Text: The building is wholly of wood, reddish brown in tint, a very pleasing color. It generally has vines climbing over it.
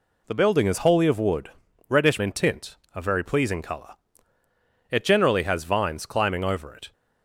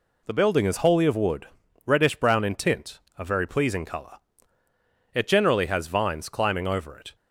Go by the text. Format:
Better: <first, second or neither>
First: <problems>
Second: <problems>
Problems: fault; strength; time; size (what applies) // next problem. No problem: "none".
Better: second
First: skips "brown"; at 2.1 s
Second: none